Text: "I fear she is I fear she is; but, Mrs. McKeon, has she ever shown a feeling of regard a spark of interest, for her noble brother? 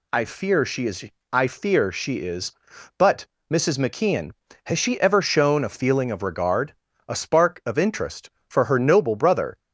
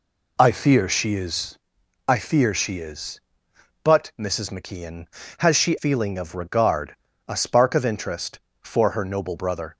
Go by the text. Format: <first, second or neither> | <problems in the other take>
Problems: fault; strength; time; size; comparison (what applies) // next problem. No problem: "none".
first | pauses between "is" and "I"; noticeable; at 1.5 s; 0.50 s long; slight in the first // skips "ever shown a"; at 5.7 s // pauses between "regard" and "a"; slight; at 6.9 s; 0.32 s long; slight in the first